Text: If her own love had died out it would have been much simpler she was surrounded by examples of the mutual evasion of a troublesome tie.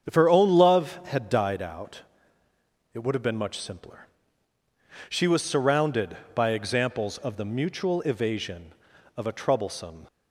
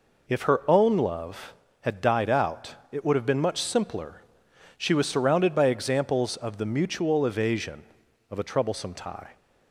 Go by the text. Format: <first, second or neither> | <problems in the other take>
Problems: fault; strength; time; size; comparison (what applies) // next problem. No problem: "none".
second | starts louder than the rest; strong; until 1.1 s; 7.5 dB // pauses between "out" and "it"; noticeable; at 2.0 s; 0.90 s long; slight in the second // pauses between "simpler" and "she"; at 4.0 s; 1.0 s long; noticeable in the second // stops before "tie"; at 10.0 s